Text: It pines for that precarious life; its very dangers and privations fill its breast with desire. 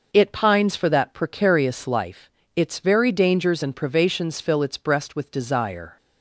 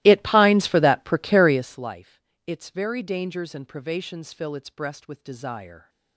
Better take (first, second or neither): first